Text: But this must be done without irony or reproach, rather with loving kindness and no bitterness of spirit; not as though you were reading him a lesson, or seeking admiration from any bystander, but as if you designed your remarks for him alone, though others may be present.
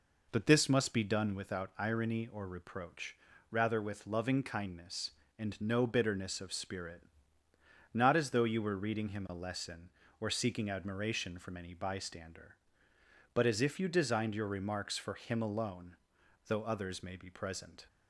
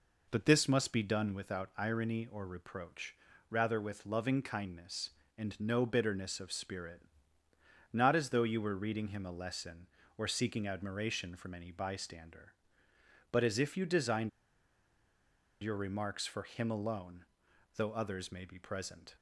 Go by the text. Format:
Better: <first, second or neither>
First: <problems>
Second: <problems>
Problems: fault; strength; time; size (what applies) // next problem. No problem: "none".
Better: first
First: none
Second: pauses between "designed" and "your"; strong; at 14.2 s; 1.3 s long